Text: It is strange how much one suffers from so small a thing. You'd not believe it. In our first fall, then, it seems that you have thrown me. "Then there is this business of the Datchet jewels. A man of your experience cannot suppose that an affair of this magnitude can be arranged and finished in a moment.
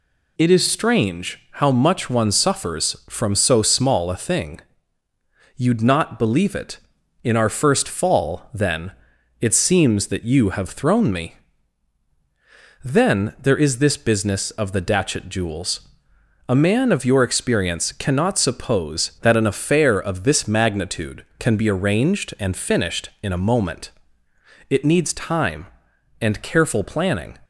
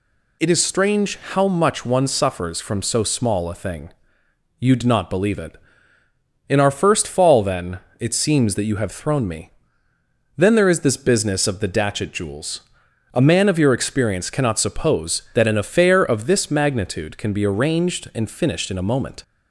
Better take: second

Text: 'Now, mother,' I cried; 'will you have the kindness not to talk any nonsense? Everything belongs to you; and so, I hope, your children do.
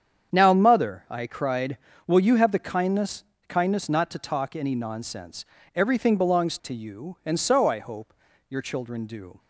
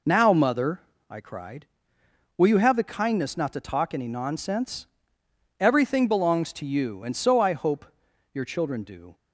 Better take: second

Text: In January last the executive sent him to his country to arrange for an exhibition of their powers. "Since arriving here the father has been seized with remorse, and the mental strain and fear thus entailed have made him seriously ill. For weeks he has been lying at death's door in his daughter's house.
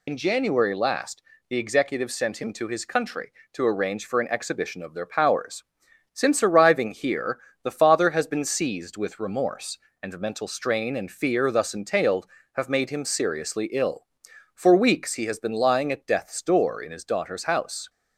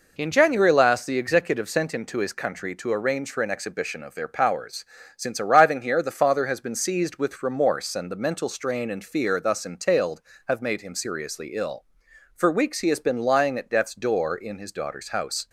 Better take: second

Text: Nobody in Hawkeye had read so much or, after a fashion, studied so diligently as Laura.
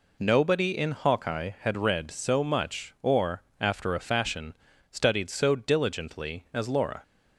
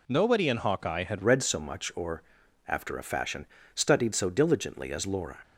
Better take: first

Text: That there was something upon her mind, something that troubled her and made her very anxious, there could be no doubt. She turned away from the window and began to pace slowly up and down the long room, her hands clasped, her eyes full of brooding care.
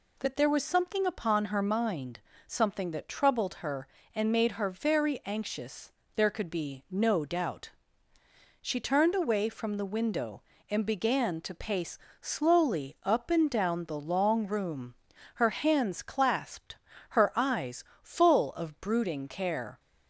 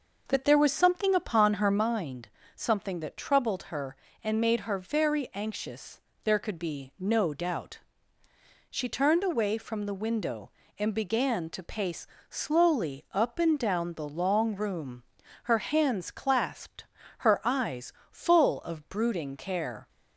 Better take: first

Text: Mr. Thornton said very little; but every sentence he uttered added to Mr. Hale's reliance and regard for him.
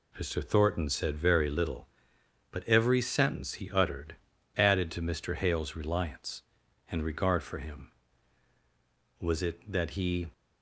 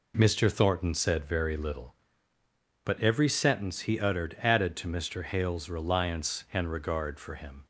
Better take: second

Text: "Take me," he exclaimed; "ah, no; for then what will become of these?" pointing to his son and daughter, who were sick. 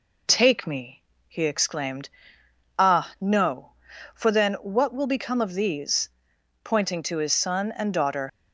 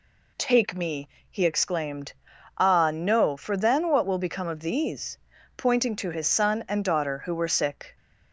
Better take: second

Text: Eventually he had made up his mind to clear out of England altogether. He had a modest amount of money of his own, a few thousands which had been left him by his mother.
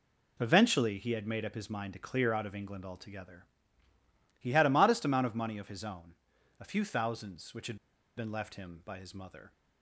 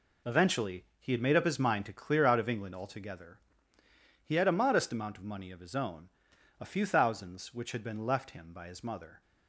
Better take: second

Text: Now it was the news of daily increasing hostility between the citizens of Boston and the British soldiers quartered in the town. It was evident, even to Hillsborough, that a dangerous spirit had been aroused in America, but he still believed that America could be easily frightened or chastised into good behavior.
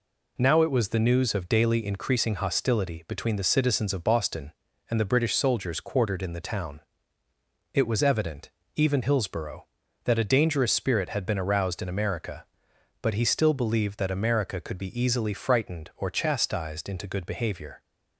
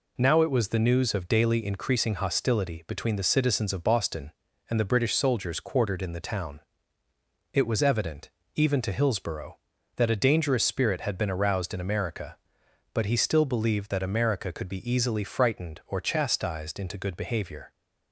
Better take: second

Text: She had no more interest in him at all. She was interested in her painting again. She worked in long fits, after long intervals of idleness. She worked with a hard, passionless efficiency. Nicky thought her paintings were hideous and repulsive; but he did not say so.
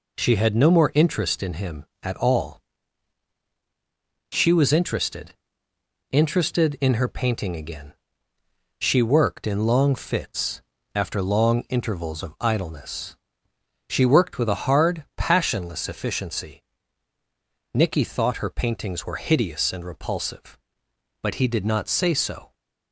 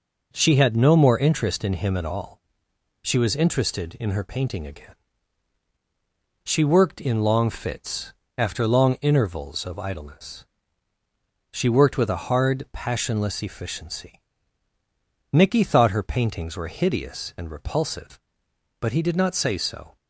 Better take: second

